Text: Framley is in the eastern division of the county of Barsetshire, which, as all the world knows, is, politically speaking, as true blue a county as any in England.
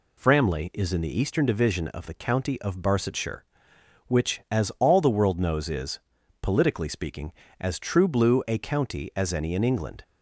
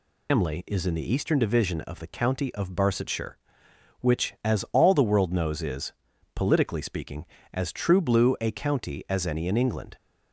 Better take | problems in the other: first | loses the start of "Framley"; at 0.2 s; 185 ms

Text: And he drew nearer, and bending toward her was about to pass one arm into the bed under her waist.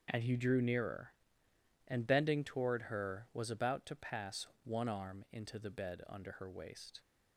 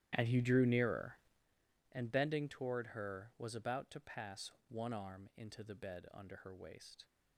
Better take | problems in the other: first | starts louder than the rest; strong; until 1.5 s; 11.5 dB // pauses between "pass" and "one"; slight; at 4.5 s; 0.16 s long; slight in the first

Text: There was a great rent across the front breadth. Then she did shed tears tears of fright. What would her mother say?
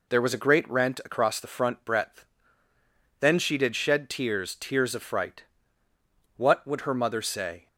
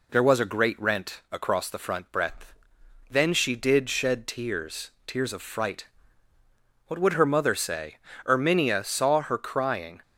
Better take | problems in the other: first | pauses between "tears" and "tears"; slight; at 4.9 s; 0.16 s long // goes on to say "Erminia saw her crying"; strong; from 8.2 s on; 1.7 s long

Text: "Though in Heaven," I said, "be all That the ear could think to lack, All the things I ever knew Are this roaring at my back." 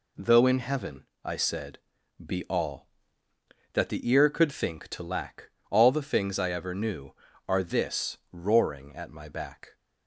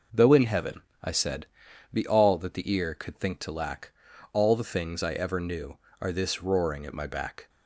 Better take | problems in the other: neither | none

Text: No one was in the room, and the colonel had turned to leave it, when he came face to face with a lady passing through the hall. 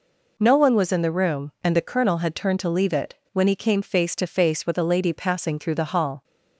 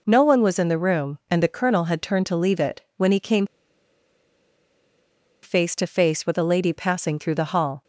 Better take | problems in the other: first | pauses between "came" and "face"; strong; at 3.4 s; 1.9 s long

